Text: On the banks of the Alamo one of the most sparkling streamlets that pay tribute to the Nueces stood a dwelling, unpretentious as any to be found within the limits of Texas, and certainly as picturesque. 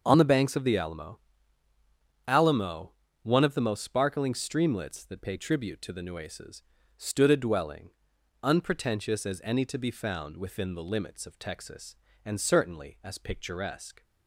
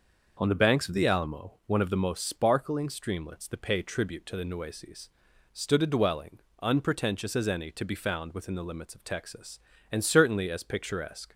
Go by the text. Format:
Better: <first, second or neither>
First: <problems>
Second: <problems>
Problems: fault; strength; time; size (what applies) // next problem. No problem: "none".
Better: second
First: starts louder than the rest; until 1.0 s; 6.5 dB // says "Alamo" twice; at 2.2 s // pauses between "Nueces" and "stood"; slight; at 6.6 s; 0.36 s long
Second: starts louder than the rest; noticeable; until 1.4 s; 6 dB // pauses between "Nueces" and "stood"; at 5.0 s; 0.42 s long